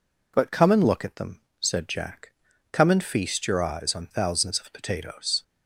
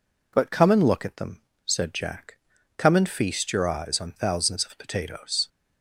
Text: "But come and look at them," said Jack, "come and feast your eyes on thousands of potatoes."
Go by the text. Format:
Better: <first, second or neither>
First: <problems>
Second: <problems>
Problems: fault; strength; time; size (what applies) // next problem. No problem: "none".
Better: neither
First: none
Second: none